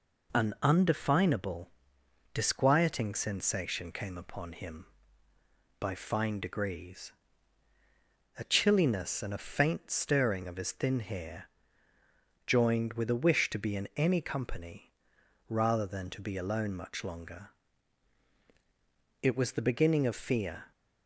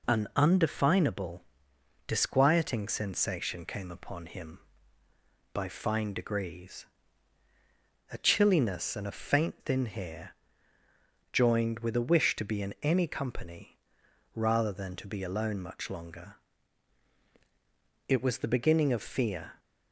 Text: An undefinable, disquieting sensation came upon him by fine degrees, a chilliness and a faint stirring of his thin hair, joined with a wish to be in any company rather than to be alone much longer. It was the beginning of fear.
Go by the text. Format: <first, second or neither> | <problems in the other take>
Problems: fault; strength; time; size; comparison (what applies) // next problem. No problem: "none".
first | skips "stirring of his"; at 9.6 s // pauses between "company" and "rather"; noticeable; at 13.7 s; 0.56 s long; noticeable in the first